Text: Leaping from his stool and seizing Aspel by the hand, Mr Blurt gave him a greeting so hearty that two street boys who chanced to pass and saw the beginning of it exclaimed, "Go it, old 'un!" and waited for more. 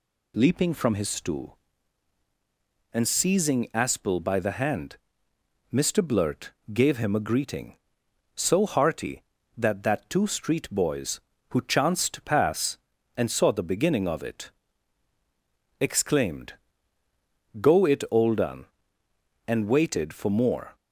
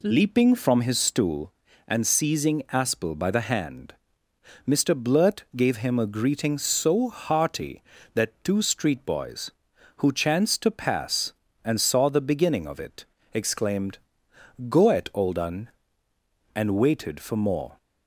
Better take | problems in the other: second | pauses between "Blurt" and "gave"; slight; at 6.5 s; 0.22 s long // says "that" twice; at 9.8 s // pauses between "it" and "exclaimed"; strong; at 14.4 s; 1.3 s long; slight in the second

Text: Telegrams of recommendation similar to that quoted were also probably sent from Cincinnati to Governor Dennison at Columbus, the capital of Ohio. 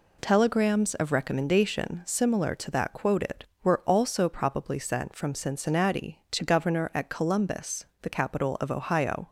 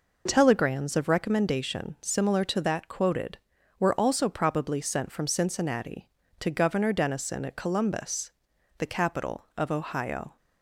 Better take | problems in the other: second | skips "Dennison"; at 6.9 s

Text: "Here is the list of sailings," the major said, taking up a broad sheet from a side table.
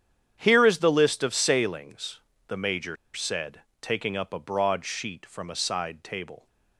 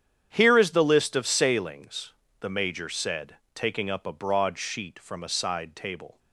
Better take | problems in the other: second | starts louder than the rest; strong; until 1.4 s; 9 dB; strong in the second // pauses between "major" and "said"; slight; at 2.9 s; 0.19 s long

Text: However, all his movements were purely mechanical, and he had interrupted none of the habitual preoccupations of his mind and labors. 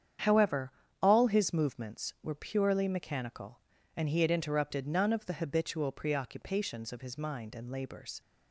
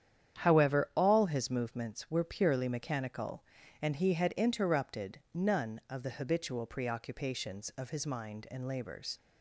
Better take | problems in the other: neither | starts louder than the rest; strong; the same in both

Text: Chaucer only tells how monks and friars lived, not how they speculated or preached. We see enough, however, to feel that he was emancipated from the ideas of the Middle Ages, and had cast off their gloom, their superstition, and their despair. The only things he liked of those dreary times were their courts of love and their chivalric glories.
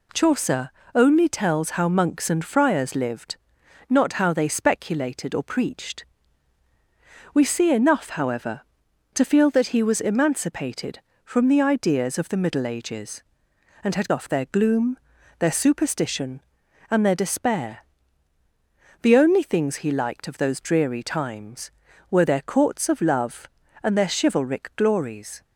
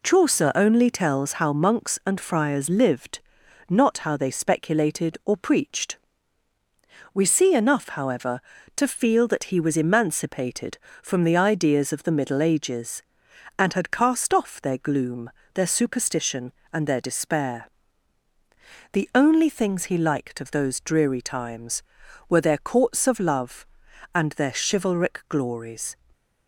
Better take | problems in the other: second | pauses between "Chaucer" and "only"; slight; at 0.7 s; 0.24 s long // skips "cast"; at 14.1 s

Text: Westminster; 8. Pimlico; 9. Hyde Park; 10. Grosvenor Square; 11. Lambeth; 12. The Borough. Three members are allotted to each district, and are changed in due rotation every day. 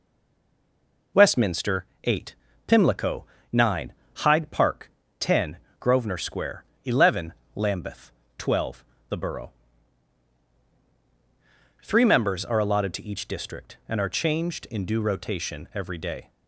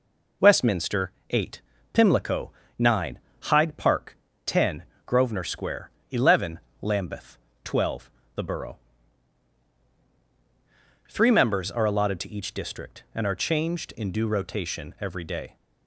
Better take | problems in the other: second | stays silent before the first word; until 1.1 s; 1.1 s long

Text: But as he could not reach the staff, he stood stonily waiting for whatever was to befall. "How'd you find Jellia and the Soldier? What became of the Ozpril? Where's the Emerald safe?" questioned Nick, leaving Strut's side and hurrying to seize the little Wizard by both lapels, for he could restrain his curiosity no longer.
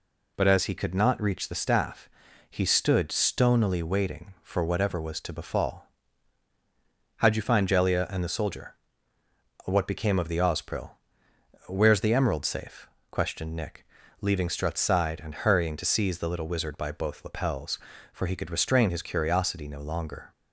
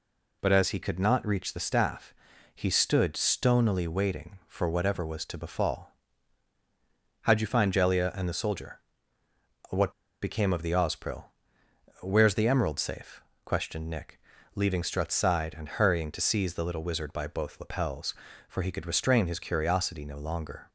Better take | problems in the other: first | pauses between "What" and "became"; slight; at 9.9 s; 0.30 s long

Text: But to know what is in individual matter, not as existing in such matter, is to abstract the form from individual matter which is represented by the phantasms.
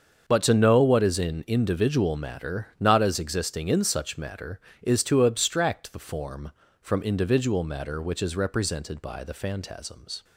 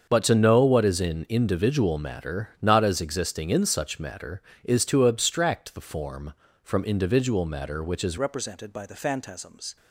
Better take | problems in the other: first | starts louder than the rest; until 1.1 s; 7 dB; also in the first // changes voice at "represented"; from 8.1 s on; 1.6 s long

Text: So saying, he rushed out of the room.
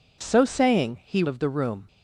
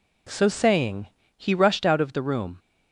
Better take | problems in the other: second | skips "rushed out"; at 1.2 s

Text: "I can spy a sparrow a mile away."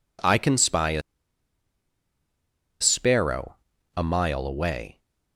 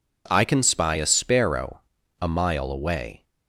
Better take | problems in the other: second | pauses between "a" and "sparrow"; strong; at 1.0 s; 1.7 s long // pauses between "sparrow" and "a"; at 3.5 s; 0.40 s long; also in the second

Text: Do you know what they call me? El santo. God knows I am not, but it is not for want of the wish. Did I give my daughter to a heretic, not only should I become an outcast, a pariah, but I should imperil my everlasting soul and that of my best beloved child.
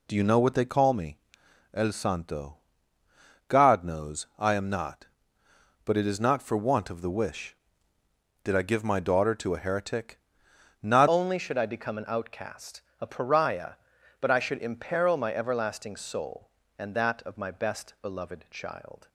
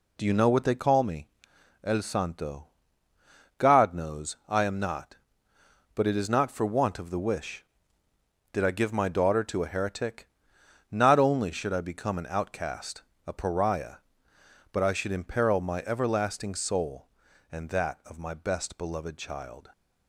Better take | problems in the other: second | changes voice at "only"; from 11.0 s on; 8.0 s long

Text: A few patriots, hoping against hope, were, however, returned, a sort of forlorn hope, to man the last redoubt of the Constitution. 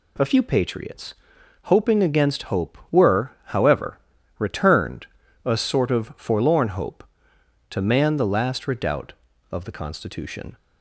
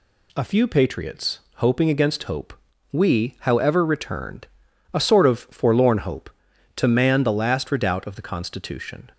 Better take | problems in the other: first | says "we" for "were"; at 2.9 s

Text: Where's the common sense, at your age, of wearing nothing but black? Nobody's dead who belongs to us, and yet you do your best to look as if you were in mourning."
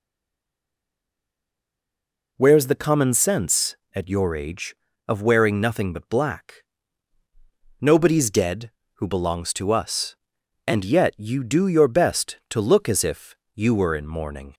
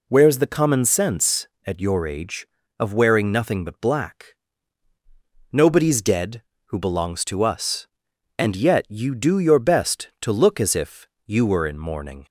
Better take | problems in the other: second | stays silent before the first word; until 2.3 s; 2.3 s long // pauses between "if" and "you"; slight; at 13.3 s; 0.18 s long; slight in the second

